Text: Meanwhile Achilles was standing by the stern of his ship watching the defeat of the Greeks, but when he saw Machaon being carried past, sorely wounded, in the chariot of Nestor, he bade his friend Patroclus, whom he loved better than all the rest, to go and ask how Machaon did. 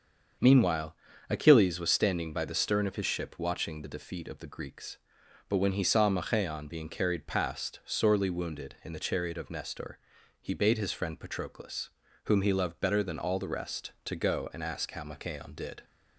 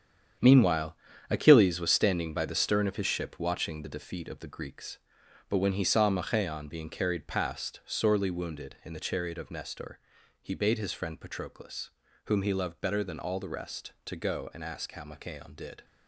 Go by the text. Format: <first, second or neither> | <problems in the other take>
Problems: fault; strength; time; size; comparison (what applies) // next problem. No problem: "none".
first | gets quieter; strong; throughout; 9 dB // starts louder than the rest; strong; until 1.7 s; 8.5 dB; also in the first // pauses between "Meanwhile" and "Achilles"; slight; at 0.9 s; 0.34 s long; slight in the first